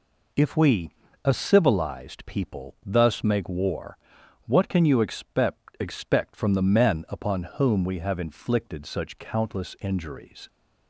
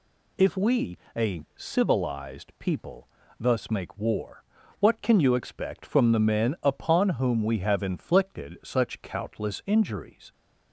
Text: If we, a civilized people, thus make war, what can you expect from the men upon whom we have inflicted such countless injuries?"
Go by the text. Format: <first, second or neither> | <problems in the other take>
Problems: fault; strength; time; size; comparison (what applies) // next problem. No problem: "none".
second | says "expect" twice; at 5.7 s // pauses between "upon" and "whom"; slight; at 7.4 s; 0.16 s long